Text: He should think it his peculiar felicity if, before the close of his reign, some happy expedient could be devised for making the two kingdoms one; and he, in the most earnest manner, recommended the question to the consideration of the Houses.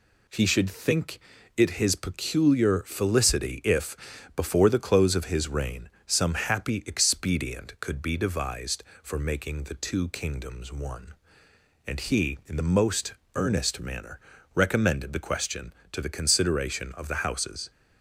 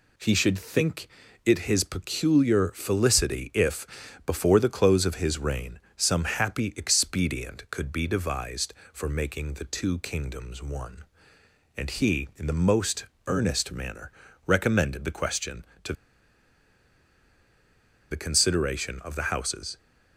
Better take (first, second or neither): first